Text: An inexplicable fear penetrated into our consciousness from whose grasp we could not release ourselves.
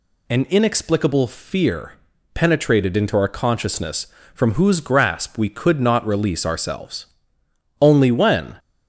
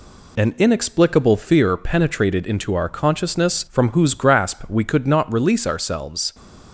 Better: second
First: pauses between "fear" and "penetrated"; at 1.9 s; 0.39 s long // goes on to say "Only when"; noticeable; from 7.8 s on; 0.76 s long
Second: none

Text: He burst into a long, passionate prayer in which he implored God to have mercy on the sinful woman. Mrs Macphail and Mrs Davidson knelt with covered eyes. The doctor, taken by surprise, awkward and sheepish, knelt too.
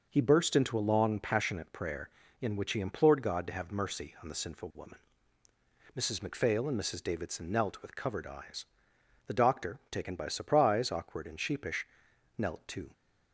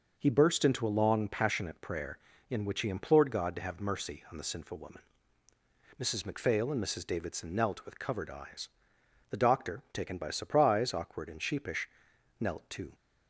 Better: neither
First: none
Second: none

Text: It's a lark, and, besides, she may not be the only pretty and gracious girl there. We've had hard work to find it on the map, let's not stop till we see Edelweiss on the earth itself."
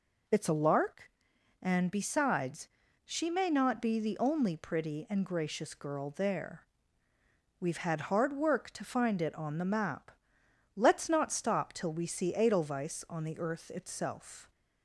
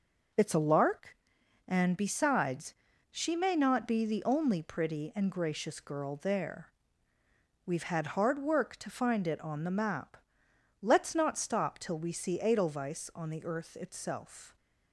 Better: first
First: none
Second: gets quieter; throughout; 6.5 dB

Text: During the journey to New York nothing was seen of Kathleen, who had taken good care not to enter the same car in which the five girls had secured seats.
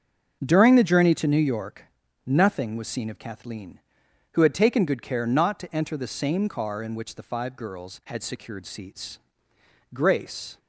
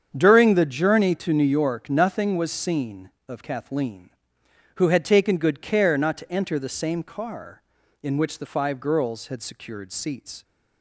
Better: second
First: starts louder than the rest; until 1.4 s; 6.5 dB // pauses between "York" and "nothing"; at 1.8 s; 0.38 s long // goes on to say "Grace"; noticeable; from 9.9 s on; 0.64 s long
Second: starts louder than the rest; strong; until 1.1 s; 7.5 dB

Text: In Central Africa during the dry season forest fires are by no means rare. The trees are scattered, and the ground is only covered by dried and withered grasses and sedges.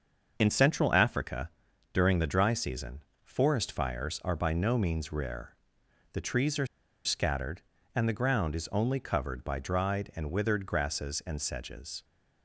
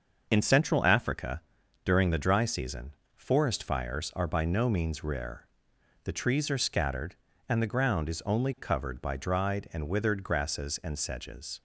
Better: second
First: starts louder than the rest; until 1.3 s; 6.5 dB // pauses between "Africa" and "during"; noticeable; at 1.4 s; 0.46 s long // pauses between "season" and "forest"; slight; at 3.0 s; 0.22 s long // pauses between "are" and "scattered"; at 6.6 s; 0.38 s long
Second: starts louder than the rest; until 1.3 s; 6.5 dB // pauses between "Africa" and "during"; noticeable; at 1.3 s; 0.46 s long // pauses between "season" and "forest"; slight; at 2.9 s; 0.22 s long

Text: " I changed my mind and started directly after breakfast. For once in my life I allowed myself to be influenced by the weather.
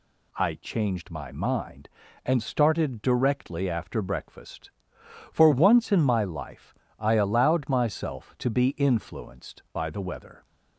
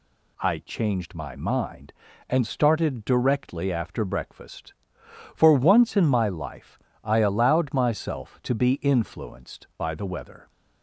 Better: neither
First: pauses between "life" and "I"; slight; at 6.7 s; 0.28 s long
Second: pauses between "life" and "I"; slight; at 6.7 s; 0.28 s long

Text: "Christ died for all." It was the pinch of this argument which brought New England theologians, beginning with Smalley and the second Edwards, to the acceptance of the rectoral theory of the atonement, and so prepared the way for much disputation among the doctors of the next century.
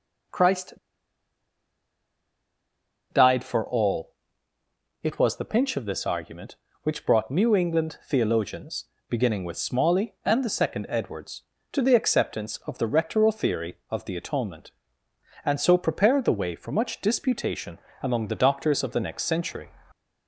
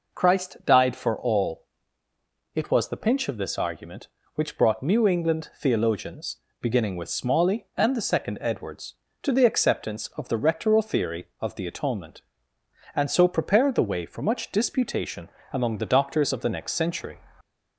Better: second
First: pauses between "Christ" and "died"; strong; at 0.7 s; 2.3 s long // pauses between "disputation" and "among"; slight; at 17.7 s; 0.24 s long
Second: pauses between "disputation" and "among"; slight; at 15.2 s; 0.24 s long

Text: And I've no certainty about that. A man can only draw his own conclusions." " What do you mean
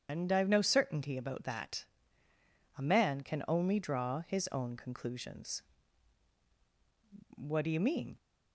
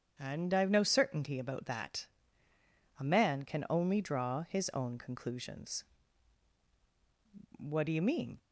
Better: second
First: loses the start of "And"; at 0.0 s; 125 ms // starts louder than the rest; strong; until 1.1 s; 9 dB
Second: starts louder than the rest; strong; until 1.1 s; 8.5 dB

